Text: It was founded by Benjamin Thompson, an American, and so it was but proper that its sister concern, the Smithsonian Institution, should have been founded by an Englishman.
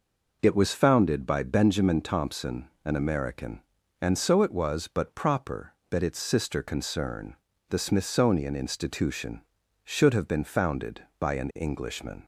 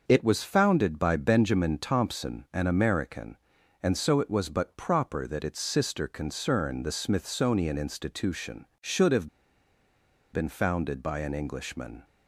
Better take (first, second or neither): first